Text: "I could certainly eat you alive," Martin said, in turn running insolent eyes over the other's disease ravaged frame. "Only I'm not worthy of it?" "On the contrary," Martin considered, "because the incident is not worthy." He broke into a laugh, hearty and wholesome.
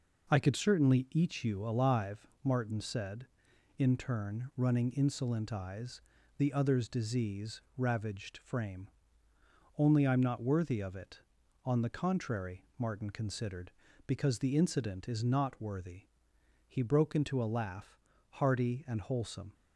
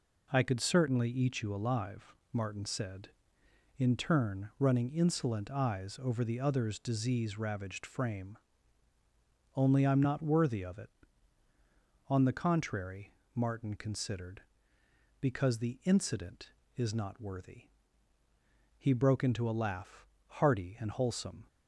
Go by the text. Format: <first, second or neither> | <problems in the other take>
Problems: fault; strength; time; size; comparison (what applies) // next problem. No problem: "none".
second | skips "over"; at 6.1 s // pauses between "disease" and "ravaged"; slight; at 7.6 s; 0.16 s long